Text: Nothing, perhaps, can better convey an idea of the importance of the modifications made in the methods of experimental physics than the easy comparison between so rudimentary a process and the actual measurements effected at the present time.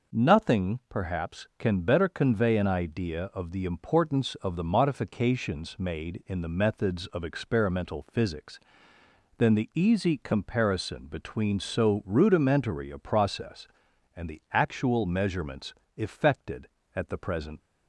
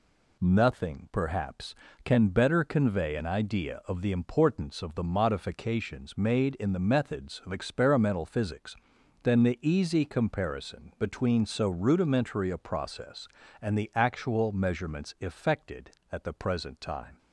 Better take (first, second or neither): second